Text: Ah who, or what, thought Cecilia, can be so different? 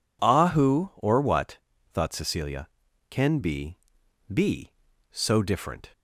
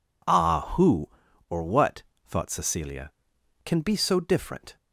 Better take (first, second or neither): second